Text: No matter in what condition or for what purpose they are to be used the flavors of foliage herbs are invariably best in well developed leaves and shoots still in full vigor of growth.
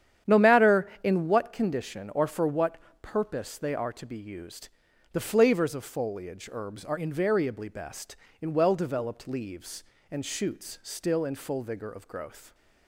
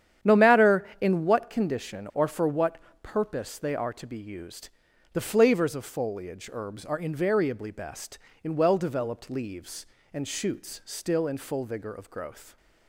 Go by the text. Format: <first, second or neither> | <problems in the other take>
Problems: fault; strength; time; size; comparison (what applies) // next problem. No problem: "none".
neither | starts louder than the rest; strong; the same in both // pauses between "what" and "purpose"; slight; the same in both // pauses between "used" and "the"; the same in both